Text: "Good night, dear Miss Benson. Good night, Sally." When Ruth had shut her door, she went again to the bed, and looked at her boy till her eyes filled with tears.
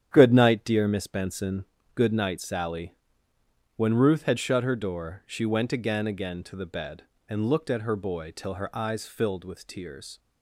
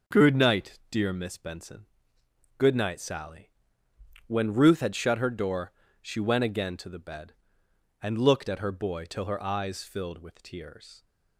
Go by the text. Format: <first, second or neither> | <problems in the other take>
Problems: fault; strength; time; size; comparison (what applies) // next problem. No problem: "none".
second | starts louder than the rest; strong; until 1.1 s; 9 dB; also in the second // says "again" twice; at 6.0 s